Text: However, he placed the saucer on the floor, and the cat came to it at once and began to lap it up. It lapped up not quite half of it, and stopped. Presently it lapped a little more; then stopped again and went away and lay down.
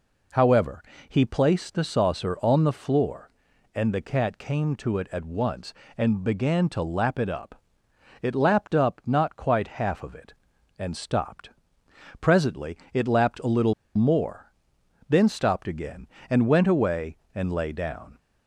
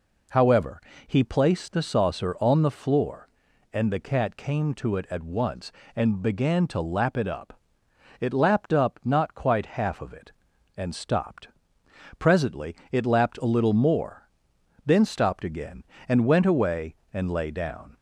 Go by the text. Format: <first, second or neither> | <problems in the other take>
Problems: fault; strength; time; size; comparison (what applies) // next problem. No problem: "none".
second | pauses between "Presently" and "it"; slight; at 12.7 s; 0.16 s long; slight in the second // pauses between "little" and "more"; slight; at 13.7 s; 0.24 s long